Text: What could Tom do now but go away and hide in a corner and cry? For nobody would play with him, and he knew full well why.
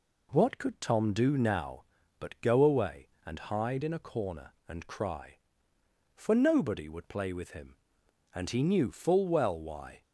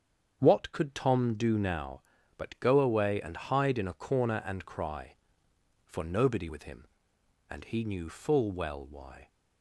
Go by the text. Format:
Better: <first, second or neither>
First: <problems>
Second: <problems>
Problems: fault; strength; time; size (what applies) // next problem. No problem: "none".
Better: first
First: none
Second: starts louder than the rest; strong; until 1.4 s; 7.5 dB // skips "would play"; at 6.4 s